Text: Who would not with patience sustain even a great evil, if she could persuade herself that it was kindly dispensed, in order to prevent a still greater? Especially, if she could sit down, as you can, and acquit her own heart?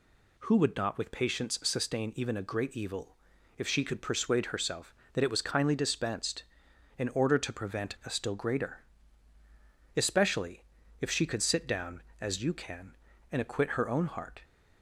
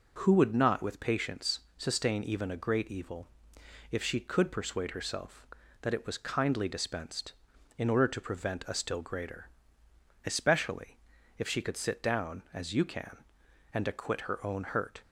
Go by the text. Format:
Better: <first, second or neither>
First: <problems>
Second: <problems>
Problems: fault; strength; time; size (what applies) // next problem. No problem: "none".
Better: first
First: none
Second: pauses between "patience" and "sustain"; slight; at 1.5 s; 0.18 s long // says "hurt" for "heart"; at 14.6 s